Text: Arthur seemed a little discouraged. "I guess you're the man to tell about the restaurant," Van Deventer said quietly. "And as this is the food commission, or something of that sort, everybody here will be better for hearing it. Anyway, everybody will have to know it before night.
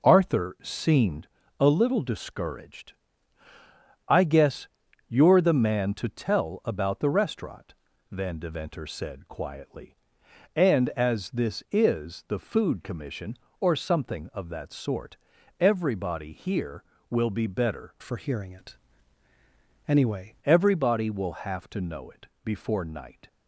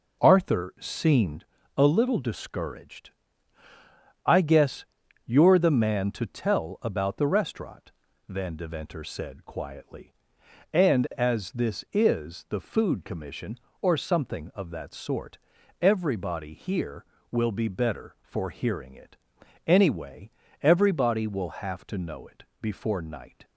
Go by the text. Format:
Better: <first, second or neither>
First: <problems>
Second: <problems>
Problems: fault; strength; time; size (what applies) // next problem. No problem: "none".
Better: second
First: pauses between "seemed" and "a"; slight; at 1.2 s; 0.32 s long // pauses between "guess" and "you're"; at 4.6 s; 0.40 s long // changes voice from "for" to "Anyway"; from 18.0 to 20.3 s; 2.3 s long // pauses between "it" and "before"; slight; at 22.2 s; 0.16 s long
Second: pauses between "seemed" and "a"; slight; at 1.4 s; 0.32 s long // pauses between "guess" and "you're"; at 4.8 s; 0.40 s long // pauses between "it" and "before"; slight; at 22.4 s; 0.16 s long